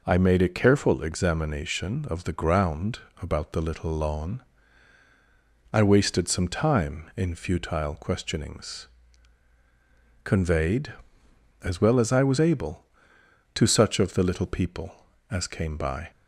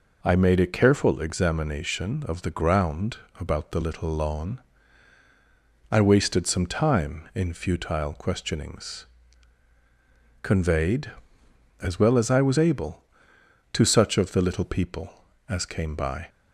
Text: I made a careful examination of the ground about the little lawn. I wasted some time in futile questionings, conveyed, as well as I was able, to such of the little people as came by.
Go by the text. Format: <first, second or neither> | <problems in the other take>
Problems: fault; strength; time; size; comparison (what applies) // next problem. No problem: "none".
neither | pauses between "ground" and "about"; slight; the same in both